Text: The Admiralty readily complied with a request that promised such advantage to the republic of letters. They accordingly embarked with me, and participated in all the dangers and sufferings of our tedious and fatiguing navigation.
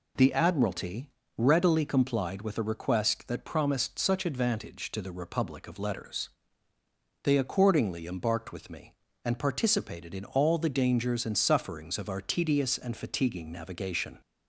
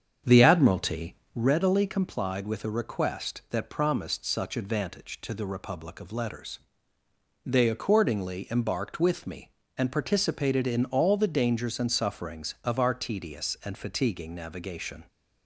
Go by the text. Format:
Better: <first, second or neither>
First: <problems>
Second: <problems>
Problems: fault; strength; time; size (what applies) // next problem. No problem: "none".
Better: first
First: pauses between "Admiralty" and "readily"; slight; at 1.1 s; 0.26 s long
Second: starts louder than the rest; strong; until 1.5 s; 7.5 dB // pauses between "Admiralty" and "readily"; slight; at 1.1 s; 0.20 s long